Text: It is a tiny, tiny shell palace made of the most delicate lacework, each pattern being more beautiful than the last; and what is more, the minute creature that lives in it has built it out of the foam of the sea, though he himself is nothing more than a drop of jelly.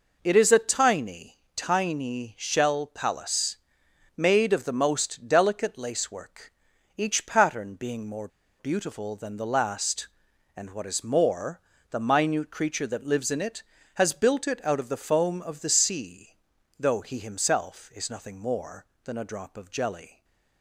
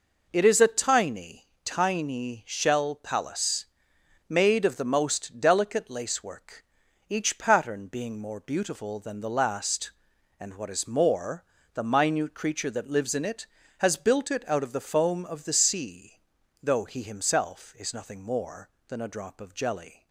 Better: second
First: pauses between "palace" and "made"; noticeable; at 3.5 s; 0.62 s long // pauses between "more" and "beautiful"; slight; at 8.2 s; 0.31 s long // stays silent after the last word; slight; from 20.1 s on; 0.5 s long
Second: pauses between "palace" and "made"; noticeable; at 3.6 s; 0.65 s long

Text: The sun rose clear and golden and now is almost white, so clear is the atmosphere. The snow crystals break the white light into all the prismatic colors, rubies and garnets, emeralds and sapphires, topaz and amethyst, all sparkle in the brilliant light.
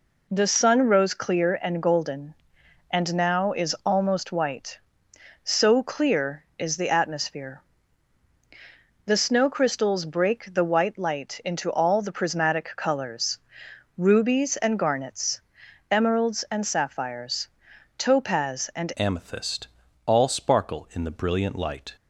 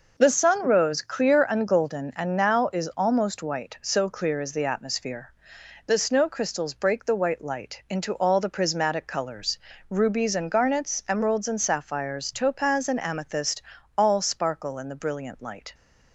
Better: second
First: changes voice at "amethyst"; from 18.9 s on; 3.0 s long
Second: none

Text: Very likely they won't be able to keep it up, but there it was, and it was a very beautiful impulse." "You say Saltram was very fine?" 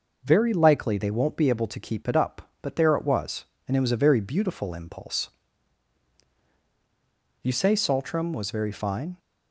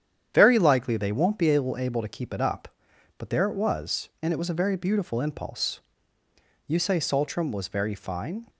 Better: first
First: none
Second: starts louder than the rest; strong; until 1.3 s; 9 dB // says "able" twice; at 1.7 s

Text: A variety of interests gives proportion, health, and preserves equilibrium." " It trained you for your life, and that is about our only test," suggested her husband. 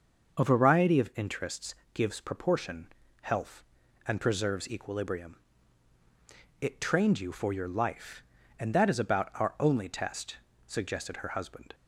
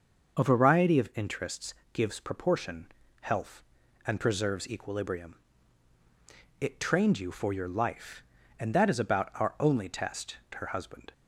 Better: first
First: starts louder than the rest; until 1.4 s; 6.5 dB // pauses between "interests" and "gives"; slight; at 1.7 s; 0.18 s long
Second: starts louder than the rest; until 1.4 s; 6.5 dB // pauses between "interests" and "gives"; slight; at 1.7 s; 0.18 s long // skips "suggested"; at 10.4 s

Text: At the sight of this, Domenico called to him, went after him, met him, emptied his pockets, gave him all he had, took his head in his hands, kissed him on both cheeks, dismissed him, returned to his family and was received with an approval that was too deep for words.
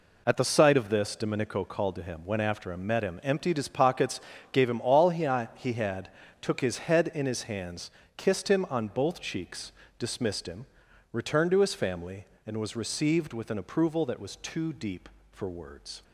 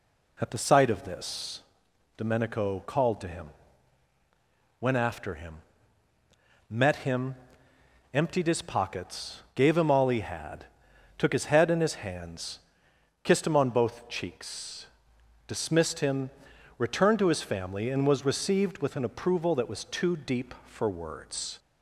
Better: second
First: says "he" twice; at 5.5 s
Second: none

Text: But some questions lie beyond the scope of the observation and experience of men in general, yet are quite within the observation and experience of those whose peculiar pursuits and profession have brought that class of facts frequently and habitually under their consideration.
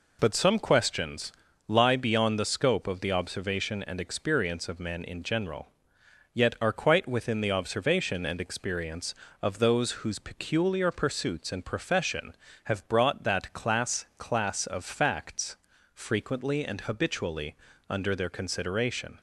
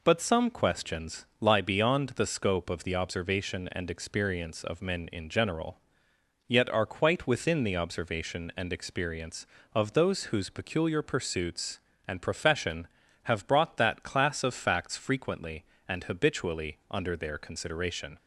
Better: second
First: pauses between "questions" and "lie"; slight; at 1.3 s; 0.34 s long // says "class" twice; at 14.1 s // pauses between "facts" and "frequently"; at 15.5 s; 0.38 s long // pauses between "habitually" and "under"; slight; at 17.5 s; 0.32 s long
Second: none

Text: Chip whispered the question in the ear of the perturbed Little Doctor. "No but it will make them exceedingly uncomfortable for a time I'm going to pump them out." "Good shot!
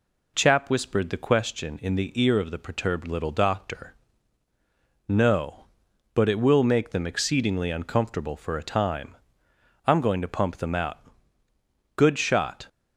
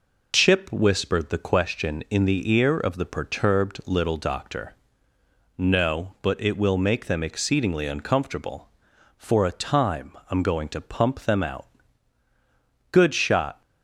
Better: second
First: says "Chap" for "Chip"; at 0.3 s // pauses between "time" and "I'm"; noticeable; at 9.1 s; 0.72 s long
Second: pauses between "time" and "I'm"; slight; at 10.1 s; 0.18 s long

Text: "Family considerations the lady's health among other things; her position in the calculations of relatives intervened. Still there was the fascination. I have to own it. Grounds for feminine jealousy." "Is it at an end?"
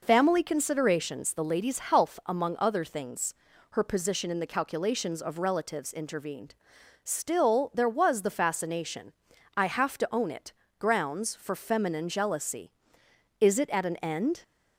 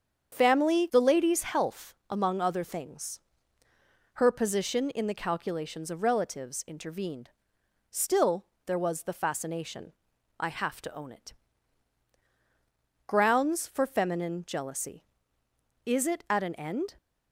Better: first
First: none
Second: starts louder than the rest; strong; until 1.3 s; 7.5 dB // skips "considerations"; at 0.8 s // pauses between "health" and "among"; slight; at 1.9 s; 0.16 s long // pauses between "Still" and "there"; slight; at 8.4 s; 0.18 s long

